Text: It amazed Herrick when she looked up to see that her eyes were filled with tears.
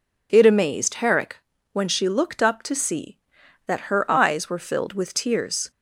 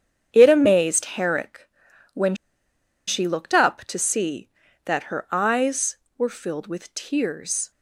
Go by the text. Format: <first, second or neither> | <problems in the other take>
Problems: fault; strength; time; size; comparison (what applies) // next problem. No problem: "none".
first | starts louder than the rest; strong; until 1.3 s; 8 dB // pauses between "Herrick" and "when"; at 1.6 s; 0.44 s long; slight in the first // pauses between "when" and "she"; noticeable; at 2.3 s; 0.72 s long